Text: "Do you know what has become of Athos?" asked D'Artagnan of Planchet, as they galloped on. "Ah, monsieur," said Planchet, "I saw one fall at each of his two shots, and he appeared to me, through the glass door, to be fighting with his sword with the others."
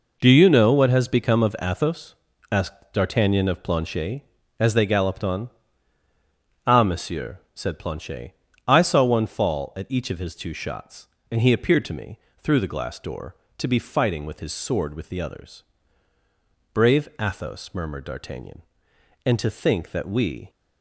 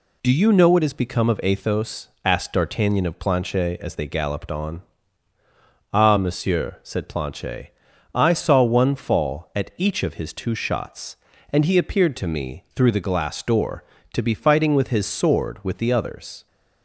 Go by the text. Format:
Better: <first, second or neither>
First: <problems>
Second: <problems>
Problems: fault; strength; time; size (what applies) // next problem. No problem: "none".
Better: second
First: goes on to say "Brave Athos murmured D'Artagnan and to think that we"; strong; from 16.7 s on; 3.7 s long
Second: none